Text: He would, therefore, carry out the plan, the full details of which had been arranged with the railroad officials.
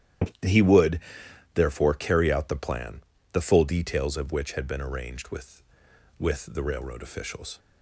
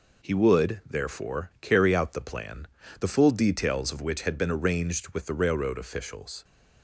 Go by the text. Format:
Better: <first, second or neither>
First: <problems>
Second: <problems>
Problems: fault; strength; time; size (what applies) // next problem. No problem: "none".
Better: second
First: starts louder than the rest; strong; until 1.9 s; 11.5 dB // says "with" twice; at 6.1 s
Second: none